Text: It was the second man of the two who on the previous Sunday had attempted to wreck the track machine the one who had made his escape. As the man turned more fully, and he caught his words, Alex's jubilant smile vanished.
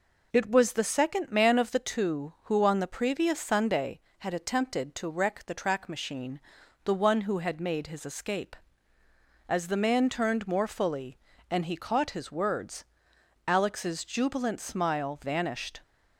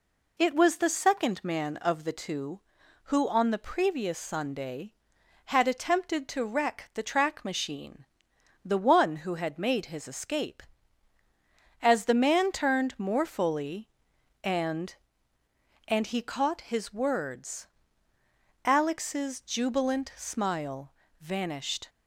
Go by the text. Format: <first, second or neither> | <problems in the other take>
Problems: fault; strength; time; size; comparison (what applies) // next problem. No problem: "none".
first | pauses between "machine" and "the"; noticeable; at 8.0 s; 0.58 s long; noticeable in the first // says "and" twice; at 15.8 s // pauses between "smile" and "vanished"; slight; at 20.9 s; 0.30 s long